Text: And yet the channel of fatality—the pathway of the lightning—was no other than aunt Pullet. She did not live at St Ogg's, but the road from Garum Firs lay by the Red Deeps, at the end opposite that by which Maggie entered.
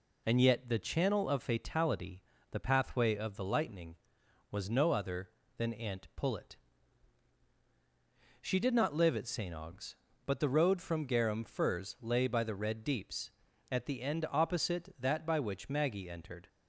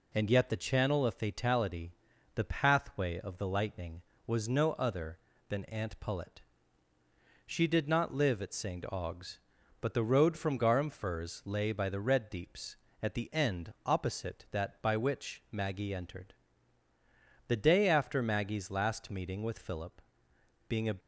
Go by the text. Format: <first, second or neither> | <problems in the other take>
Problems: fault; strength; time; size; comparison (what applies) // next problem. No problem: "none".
first | goes on to say "The day after Maggie's last meeting with Philip being a"; strong; from 17.4 s on; 3.4 s long